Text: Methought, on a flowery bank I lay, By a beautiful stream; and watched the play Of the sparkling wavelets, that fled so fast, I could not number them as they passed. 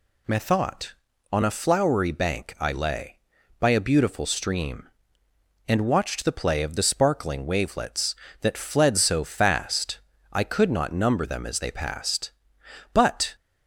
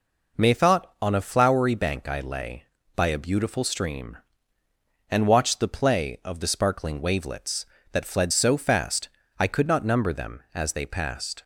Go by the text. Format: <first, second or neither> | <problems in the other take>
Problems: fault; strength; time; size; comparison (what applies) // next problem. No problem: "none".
second | goes on to say "But"; slight; from 12.9 s on; 0.42 s long